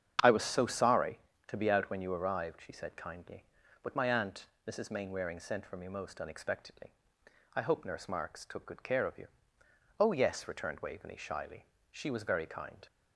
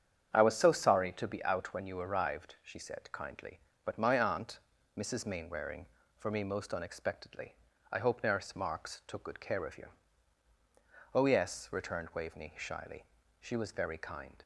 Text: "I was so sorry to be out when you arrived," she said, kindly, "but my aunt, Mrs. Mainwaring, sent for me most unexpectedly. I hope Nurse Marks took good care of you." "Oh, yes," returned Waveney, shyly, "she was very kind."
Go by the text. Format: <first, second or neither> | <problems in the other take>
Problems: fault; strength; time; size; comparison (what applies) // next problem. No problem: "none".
first | starts louder than the rest; strong; until 1.3 s; 8 dB; strong in the first // skips "sent"; at 6.0 s